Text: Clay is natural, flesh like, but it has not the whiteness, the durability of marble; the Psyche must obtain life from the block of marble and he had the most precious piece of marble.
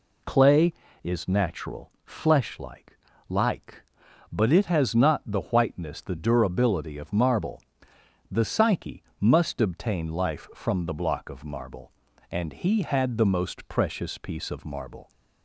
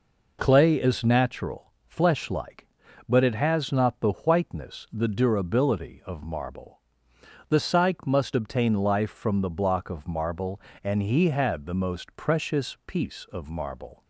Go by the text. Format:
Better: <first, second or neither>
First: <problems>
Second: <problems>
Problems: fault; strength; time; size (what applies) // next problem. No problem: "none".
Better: second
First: says "like" twice; at 3.2 s // pauses between "Psyche" and "must"; slight; at 9.0 s; 0.16 s long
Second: none